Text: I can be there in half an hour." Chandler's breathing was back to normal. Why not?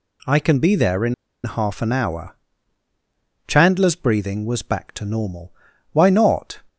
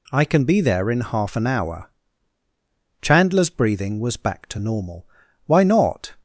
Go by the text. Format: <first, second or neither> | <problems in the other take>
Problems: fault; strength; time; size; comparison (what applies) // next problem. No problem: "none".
second | pauses between "in" and "half"; slight; at 1.1 s; 0.30 s long